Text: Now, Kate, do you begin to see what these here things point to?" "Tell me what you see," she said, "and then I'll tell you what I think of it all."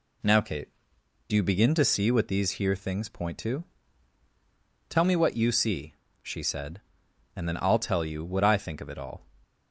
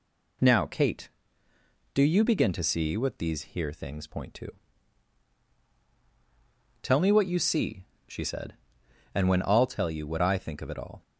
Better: first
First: none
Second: says "when" for "then"; at 9.2 s

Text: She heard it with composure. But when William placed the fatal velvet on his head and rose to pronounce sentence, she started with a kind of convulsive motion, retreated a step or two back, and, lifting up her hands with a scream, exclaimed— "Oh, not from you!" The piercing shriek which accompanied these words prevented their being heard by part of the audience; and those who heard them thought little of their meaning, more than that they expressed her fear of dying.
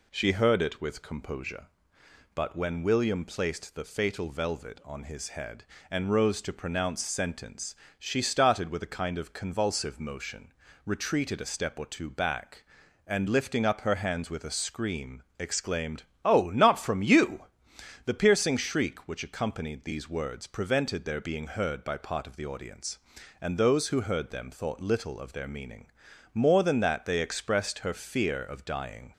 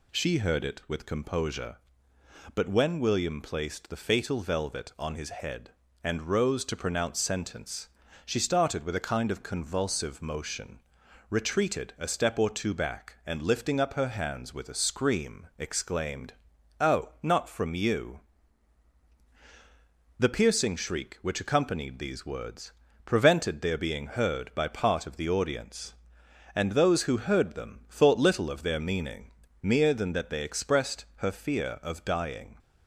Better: first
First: none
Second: pauses between "words" and "prevented"; slight; at 22.7 s; 0.32 s long // says "mere" for "more"; at 29.6 s

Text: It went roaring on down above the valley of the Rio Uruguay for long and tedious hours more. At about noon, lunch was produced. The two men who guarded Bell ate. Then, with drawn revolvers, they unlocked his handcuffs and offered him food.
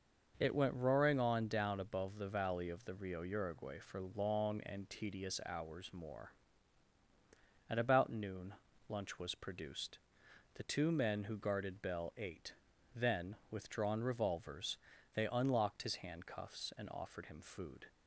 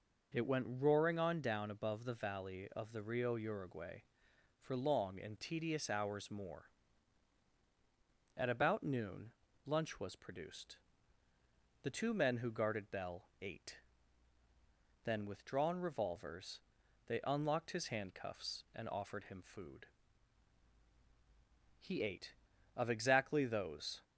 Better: first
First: none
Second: pauses between "Bell" and "ate"; slight; at 13.2 s; 0.16 s long // goes on to say "He ate of exactly those"; strong; from 21.7 s on; 2.2 s long

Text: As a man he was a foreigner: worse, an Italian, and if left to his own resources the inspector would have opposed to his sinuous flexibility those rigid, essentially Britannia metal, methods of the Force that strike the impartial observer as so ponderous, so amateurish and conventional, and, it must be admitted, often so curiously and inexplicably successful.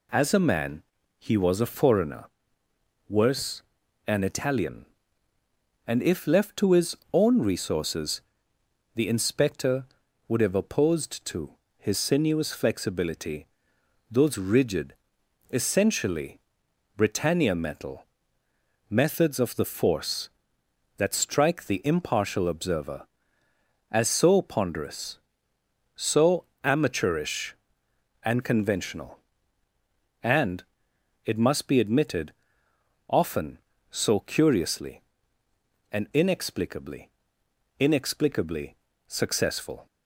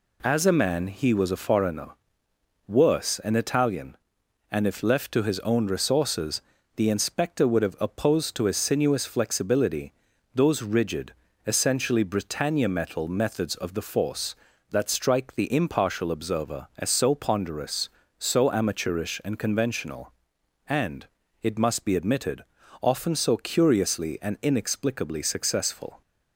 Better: second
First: pauses between "man" and "he"; slight; at 0.8 s; 0.36 s long // pauses between "his" and "own"; slight; at 6.9 s; 0.16 s long // pauses between "resources" and "the"; noticeable; at 8.2 s; 0.76 s long // pauses between "to" and "his"; slight; at 11.5 s; 0.28 s long // pauses between "flexibility" and "those"; noticeable; at 13.4 s; 0.64 s long // pauses between "essentially" and "Britannia"; noticeable; at 16.4 s; 0.56 s long // pauses between "so" and "amateurish"; slight; at 26.4 s; 0.18 s long // says "inexplicably" twice; at 37.7 s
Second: pauses between "resources" and "the"; slight; at 6.4 s; 0.32 s long // pauses between "flexibility" and "those"; at 9.9 s; 0.42 s long

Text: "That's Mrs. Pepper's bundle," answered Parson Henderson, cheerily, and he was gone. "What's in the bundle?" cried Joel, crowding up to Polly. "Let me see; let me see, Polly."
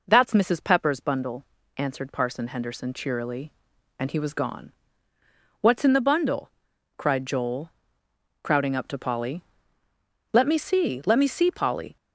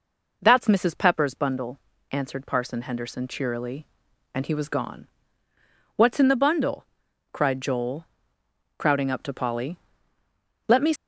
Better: first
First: none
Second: stops before "see let me see Polly"; at 10.9 s

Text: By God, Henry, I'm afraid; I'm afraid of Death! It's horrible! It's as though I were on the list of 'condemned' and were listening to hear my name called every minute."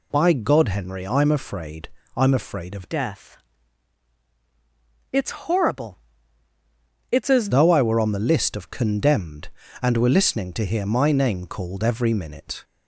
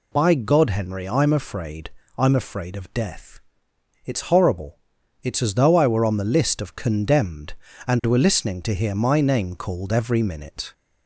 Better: second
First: changes voice from "Death" to "as"; from 2.8 to 7.4 s; 4.6 s long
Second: none

